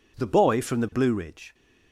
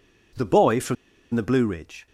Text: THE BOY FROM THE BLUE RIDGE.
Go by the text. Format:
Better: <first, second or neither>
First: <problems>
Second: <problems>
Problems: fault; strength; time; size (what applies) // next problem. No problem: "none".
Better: first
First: none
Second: pauses between "FROM" and "THE"; at 0.9 s; 0.39 s long